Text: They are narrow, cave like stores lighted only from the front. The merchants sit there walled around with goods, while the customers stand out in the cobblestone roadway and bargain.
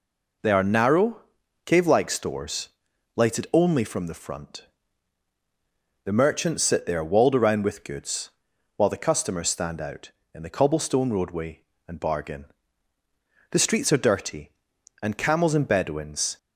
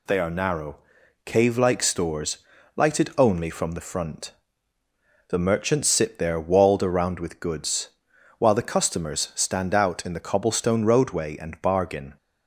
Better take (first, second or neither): second